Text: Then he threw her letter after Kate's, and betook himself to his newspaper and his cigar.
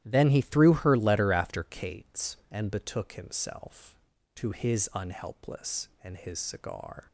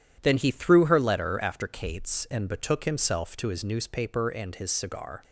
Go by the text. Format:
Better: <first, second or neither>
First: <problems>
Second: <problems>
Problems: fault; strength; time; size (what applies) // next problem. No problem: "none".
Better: second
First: starts louder than the rest; strong; until 1.0 s; 13 dB // says "unhelpless" for "newspaper"; at 4.9 s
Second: none